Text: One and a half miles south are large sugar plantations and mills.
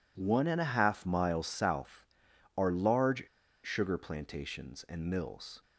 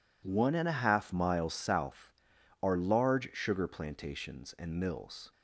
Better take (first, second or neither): second